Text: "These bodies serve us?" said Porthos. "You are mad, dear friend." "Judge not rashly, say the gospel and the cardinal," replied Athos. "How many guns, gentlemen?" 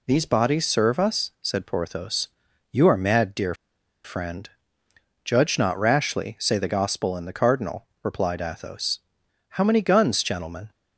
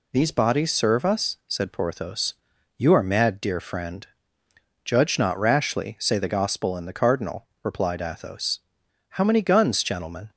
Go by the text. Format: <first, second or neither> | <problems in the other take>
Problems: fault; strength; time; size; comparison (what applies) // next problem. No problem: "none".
second | pauses between "dear" and "friend"; noticeable; at 3.5 s; 0.50 s long